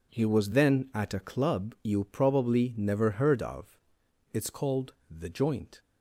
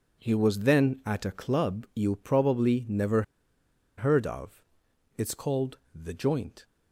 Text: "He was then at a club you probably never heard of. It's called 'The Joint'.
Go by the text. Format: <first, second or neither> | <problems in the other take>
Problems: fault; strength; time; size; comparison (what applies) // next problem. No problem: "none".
first | pauses between "never" and "heard"; noticeable; at 3.2 s; 0.75 s long // pauses between "called" and "The"; slight; at 5.7 s; 0.18 s long; slight in the first